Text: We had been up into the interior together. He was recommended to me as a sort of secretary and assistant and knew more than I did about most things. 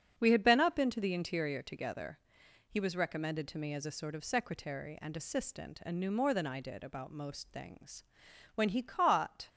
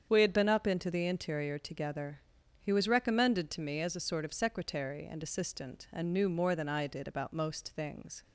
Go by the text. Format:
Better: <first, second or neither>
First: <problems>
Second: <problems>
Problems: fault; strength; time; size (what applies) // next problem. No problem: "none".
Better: second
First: starts louder than the rest; until 1.1 s; 7 dB // goes on to say "When he caught"; noticeable; from 8.5 s on; 0.94 s long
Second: starts louder than the rest; strong; until 1.1 s; 7.5 dB